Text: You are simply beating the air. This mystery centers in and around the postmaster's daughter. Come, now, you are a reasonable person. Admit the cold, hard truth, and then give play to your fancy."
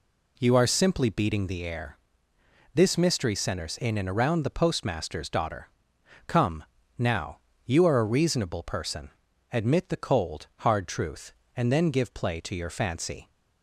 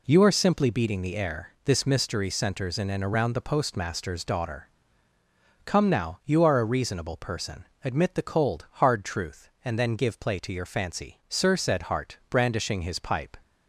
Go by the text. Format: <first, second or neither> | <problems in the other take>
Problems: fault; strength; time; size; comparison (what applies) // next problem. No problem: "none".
first | goes on to say "Sir said Hart brandishing his pipe"; strong; from 11.2 s on; 2.0 s long